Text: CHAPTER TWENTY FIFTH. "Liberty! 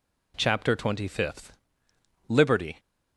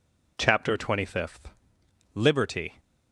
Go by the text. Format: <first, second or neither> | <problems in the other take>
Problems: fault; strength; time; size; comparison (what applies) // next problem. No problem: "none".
neither | none